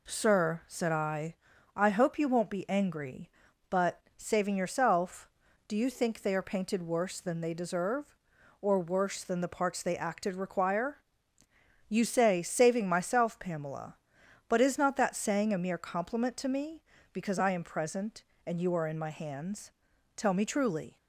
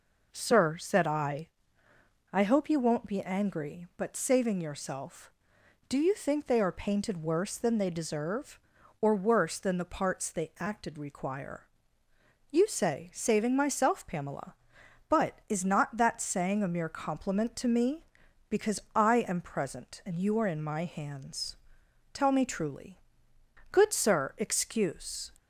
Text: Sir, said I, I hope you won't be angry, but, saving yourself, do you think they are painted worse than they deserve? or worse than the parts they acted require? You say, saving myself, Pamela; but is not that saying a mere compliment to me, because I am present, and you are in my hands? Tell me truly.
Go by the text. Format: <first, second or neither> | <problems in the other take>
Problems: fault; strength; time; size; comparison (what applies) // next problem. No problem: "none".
first | pauses between "because" and "I"; slight; at 18.7 s; 0.16 s long // goes on to say "Good sir excuse"; from 23.7 s on; 1.6 s long